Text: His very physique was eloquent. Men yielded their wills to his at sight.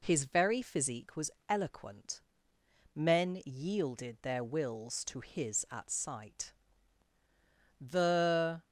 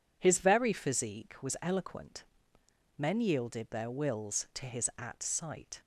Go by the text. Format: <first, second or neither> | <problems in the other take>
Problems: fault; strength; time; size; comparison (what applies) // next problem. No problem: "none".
second | pauses between "was" and "eloquent"; slight; at 1.3 s; 0.16 s long // goes on to say "The"; noticeable; from 7.7 s on; 0.84 s long